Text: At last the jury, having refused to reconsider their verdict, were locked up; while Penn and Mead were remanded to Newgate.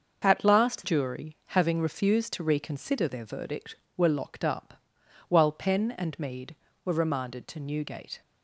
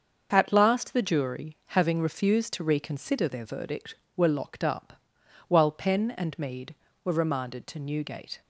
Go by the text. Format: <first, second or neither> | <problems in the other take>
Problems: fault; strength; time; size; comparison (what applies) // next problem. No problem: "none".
second | starts louder than the rest; until 1.2 s; 6.5 dB; also in the second // skips "the"; at 0.8 s